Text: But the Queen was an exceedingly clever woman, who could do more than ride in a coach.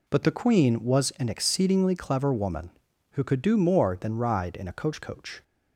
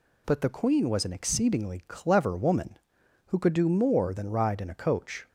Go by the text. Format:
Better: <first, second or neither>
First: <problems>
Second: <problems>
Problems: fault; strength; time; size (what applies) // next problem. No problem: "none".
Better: second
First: says "coach" twice; at 5.0 s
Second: none